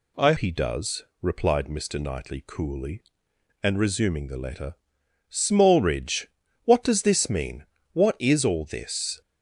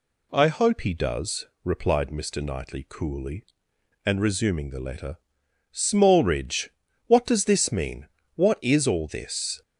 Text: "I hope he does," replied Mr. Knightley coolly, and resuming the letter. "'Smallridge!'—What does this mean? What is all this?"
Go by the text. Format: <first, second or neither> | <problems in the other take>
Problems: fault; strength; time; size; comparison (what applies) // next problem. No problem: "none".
second | skips "hope"; at 0.3 s